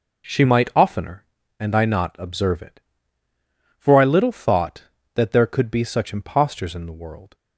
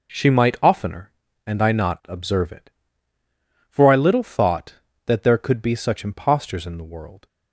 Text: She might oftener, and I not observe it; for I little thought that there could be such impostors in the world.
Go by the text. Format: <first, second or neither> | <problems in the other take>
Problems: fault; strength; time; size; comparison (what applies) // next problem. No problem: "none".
neither | none